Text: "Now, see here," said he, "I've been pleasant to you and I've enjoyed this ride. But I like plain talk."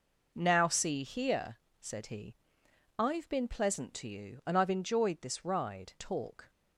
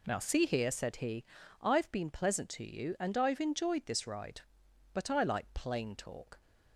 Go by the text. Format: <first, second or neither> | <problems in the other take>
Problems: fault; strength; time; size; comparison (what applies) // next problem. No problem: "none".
second | skips "But I like plain"; at 5.9 s